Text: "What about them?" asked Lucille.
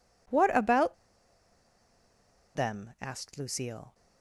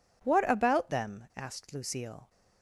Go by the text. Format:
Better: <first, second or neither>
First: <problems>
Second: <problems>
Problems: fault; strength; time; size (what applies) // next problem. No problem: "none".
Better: second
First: pauses between "about" and "them"; strong; at 0.9 s; 1.6 s long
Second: none